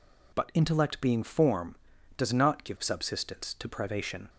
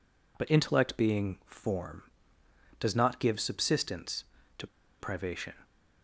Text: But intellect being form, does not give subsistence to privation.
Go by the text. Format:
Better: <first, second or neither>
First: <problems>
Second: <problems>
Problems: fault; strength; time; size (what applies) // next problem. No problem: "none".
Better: first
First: none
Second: pauses between "to" and "privation"; slight; at 4.6 s; 0.33 s long